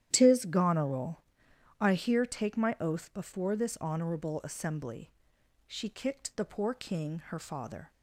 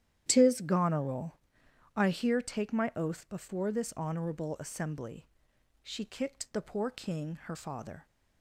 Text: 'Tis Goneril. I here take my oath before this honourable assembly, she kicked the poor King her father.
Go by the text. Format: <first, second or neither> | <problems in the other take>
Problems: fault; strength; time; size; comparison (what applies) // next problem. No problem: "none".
neither | starts louder than the rest; strong; the same in both